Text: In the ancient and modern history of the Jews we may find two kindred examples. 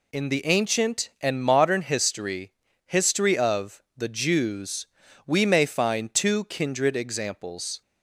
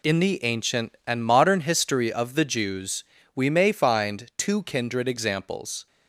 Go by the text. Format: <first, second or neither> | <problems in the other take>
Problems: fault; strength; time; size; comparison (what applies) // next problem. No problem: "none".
second | says "history" twice; at 2.8 s // pauses between "Jews" and "we"; at 4.8 s; 0.38 s long; slight in the second